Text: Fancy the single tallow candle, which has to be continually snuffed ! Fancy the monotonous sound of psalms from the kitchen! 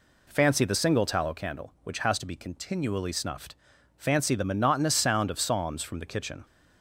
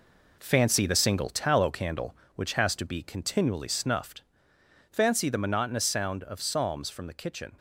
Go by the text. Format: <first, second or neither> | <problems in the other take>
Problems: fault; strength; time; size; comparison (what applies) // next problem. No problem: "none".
first | gets quieter; throughout; 7 dB